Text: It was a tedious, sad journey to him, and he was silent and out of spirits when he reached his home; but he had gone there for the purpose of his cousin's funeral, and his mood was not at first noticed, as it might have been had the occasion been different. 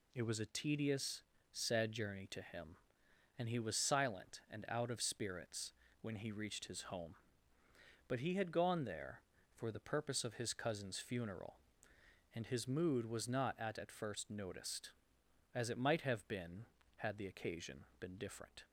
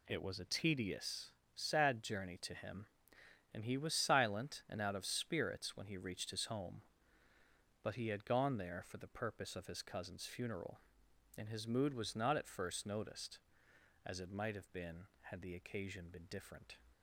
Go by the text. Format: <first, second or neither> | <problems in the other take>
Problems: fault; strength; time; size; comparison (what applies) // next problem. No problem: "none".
second | pauses between "spirits" and "when"; slight; at 5.7 s; 0.30 s long // says "at" twice; at 13.7 s // pauses between "occasion" and "been"; slight; at 17.8 s; 0.16 s long